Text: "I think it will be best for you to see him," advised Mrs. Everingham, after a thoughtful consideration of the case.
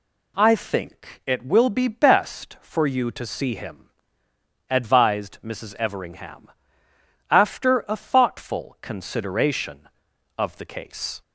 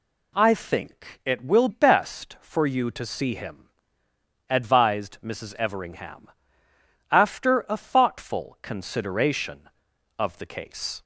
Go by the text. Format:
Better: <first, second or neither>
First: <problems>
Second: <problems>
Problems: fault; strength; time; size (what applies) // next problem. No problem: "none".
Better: first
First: none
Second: skips "be"; at 1.6 s